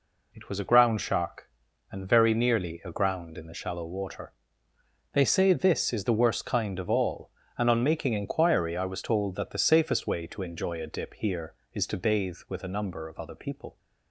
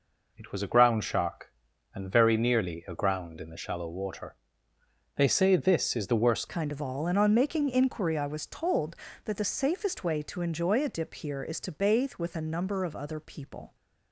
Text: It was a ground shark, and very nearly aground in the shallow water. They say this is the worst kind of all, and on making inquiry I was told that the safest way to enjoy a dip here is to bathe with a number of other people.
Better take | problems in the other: first | changes voice at "kind"; from 6.4 s on; 7.3 s long

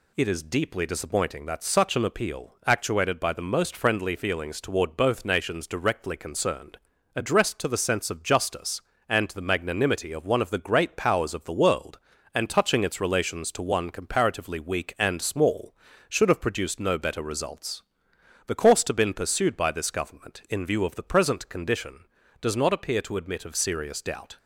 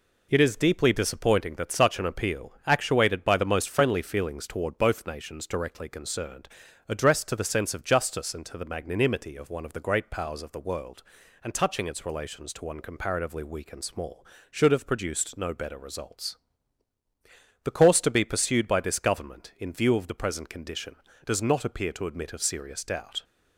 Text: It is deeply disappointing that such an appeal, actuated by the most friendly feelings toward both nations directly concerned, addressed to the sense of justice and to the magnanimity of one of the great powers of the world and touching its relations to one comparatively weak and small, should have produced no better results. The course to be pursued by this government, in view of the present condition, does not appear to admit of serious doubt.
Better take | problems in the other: second | says "been" for "be"; at 18.9 s

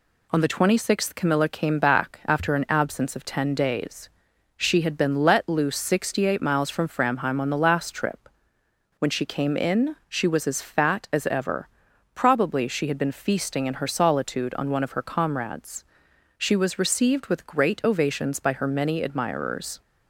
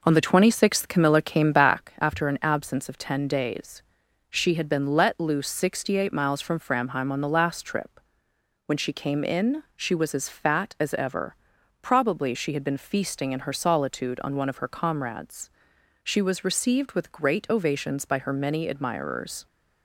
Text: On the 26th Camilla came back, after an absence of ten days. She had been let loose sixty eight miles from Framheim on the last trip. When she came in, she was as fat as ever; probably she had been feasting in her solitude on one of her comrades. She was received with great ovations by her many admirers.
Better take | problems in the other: first | starts louder than the rest; noticeable; until 1.8 s; 5 dB

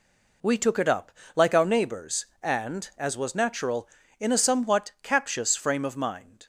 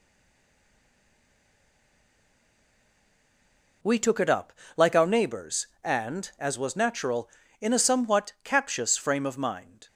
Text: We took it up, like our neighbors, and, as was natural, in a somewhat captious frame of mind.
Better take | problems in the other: first | stays silent before the first word; strong; until 3.8 s; 3.8 s long

